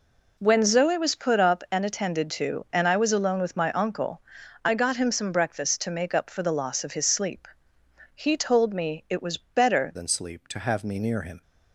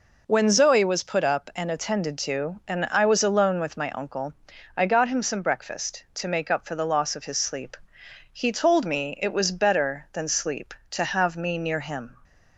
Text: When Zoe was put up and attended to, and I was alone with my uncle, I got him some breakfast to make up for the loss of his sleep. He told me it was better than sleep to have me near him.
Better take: second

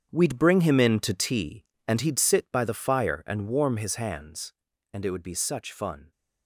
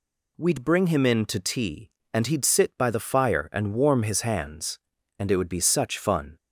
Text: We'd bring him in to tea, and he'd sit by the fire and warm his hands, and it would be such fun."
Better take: second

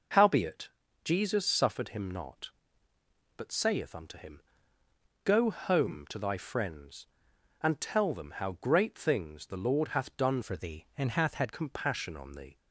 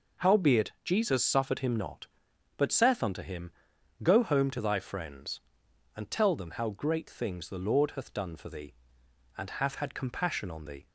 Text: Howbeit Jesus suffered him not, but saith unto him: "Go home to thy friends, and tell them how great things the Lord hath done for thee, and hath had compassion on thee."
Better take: second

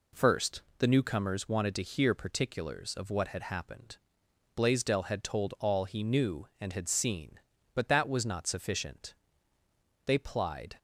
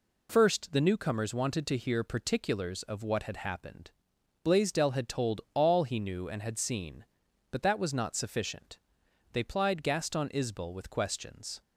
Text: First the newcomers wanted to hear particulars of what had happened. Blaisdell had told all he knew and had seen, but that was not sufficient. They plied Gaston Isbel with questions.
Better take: second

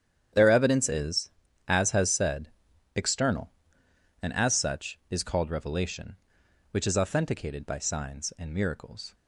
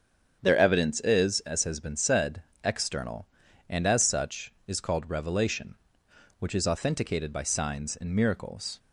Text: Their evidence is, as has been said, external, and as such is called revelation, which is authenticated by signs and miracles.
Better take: second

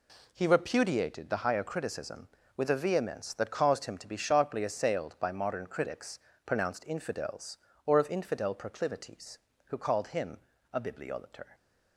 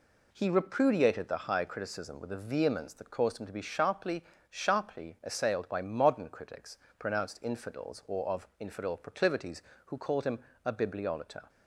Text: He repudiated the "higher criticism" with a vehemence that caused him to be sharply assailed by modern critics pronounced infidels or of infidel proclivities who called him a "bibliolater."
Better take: first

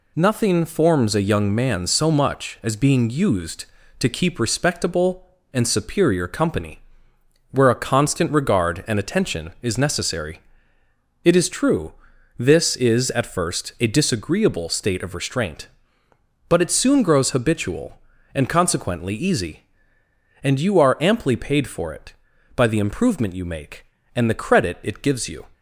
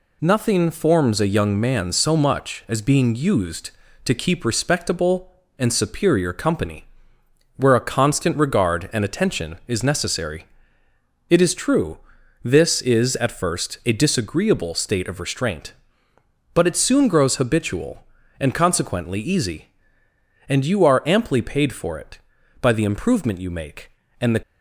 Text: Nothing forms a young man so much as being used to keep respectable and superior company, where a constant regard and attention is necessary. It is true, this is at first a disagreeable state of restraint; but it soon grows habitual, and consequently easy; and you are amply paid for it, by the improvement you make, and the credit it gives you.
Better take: first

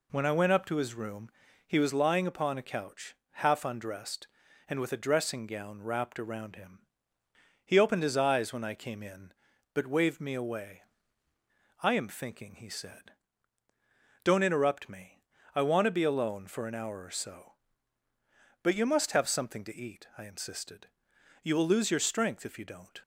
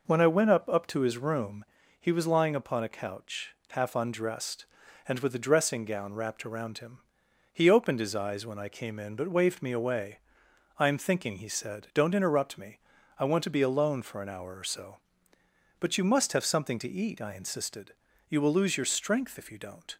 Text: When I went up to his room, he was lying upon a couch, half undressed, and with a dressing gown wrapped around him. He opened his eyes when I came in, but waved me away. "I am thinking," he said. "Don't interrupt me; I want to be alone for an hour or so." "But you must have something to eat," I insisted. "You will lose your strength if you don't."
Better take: first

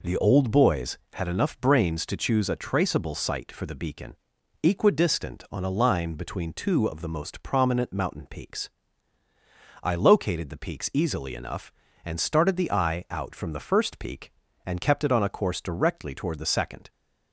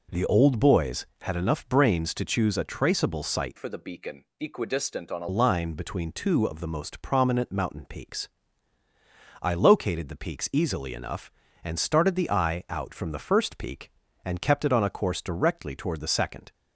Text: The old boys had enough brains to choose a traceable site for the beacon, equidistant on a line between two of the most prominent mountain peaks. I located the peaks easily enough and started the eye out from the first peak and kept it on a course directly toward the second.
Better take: first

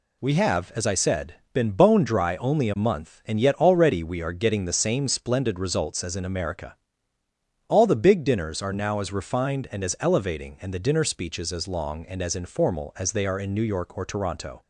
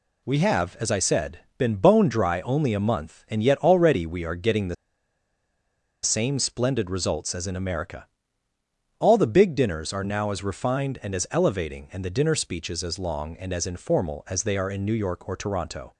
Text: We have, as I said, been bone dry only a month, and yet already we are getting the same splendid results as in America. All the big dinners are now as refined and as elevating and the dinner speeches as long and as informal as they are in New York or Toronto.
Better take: first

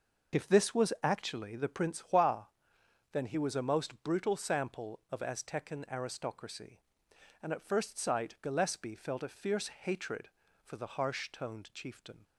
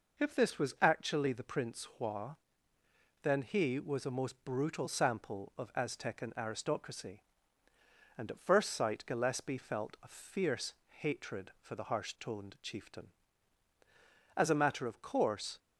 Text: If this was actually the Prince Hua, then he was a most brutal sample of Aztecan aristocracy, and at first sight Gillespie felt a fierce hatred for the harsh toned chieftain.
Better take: first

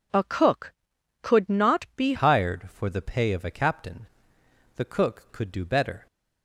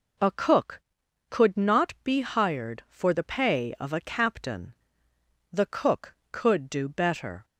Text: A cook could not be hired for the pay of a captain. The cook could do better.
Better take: second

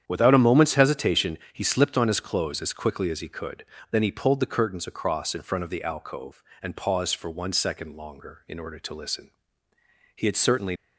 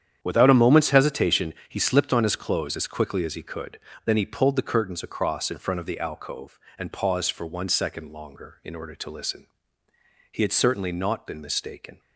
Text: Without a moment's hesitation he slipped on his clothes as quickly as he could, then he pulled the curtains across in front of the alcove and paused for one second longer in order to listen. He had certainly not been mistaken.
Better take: second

